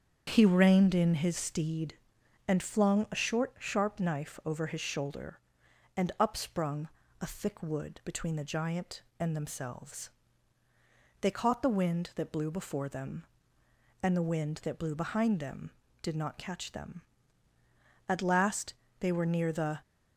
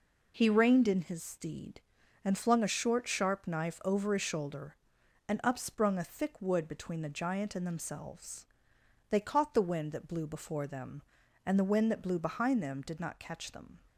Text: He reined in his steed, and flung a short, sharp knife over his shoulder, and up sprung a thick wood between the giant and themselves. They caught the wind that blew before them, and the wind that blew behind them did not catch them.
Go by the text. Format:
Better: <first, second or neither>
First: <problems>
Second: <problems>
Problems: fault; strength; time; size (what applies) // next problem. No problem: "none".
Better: second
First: starts louder than the rest; strong; until 1.2 s; 8 dB // pauses between "sprung" and "a"; slight; at 6.8 s; 0.32 s long // goes on to say "At last they were near the"; strong; from 18.0 s on; 1.7 s long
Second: none